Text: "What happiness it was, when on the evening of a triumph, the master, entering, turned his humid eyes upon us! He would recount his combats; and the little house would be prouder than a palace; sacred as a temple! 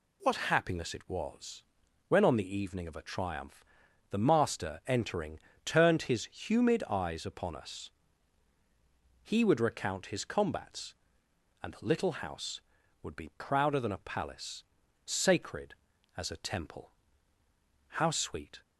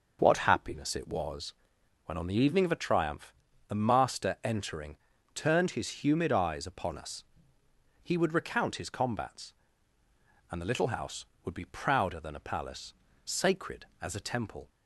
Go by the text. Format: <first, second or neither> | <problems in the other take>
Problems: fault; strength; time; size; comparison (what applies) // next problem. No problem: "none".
second | goes on to say "How sweet"; noticeable; from 17.8 s on; 0.74 s long